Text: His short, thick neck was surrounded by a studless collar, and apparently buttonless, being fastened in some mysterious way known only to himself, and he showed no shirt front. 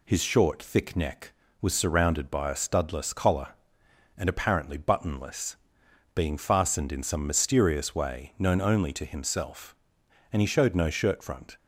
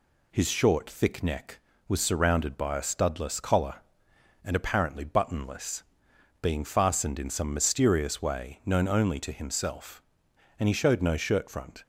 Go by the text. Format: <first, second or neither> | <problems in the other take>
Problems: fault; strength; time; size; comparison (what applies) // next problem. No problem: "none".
neither | none